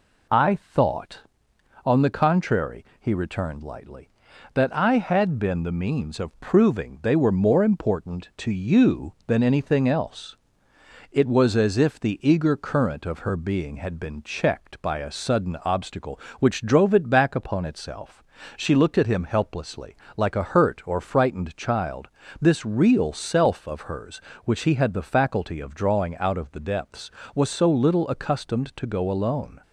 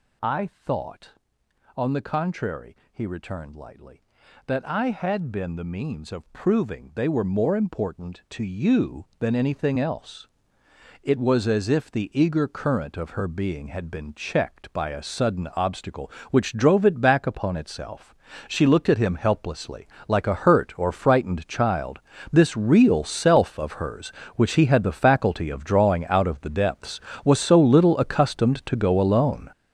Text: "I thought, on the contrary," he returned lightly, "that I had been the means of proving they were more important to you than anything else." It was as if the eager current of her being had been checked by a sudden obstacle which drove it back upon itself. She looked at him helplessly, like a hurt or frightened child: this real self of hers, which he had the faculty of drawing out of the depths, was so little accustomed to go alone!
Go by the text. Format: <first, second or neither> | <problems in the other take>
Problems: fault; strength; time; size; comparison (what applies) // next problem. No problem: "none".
first | gets louder; strong; throughout; 10 dB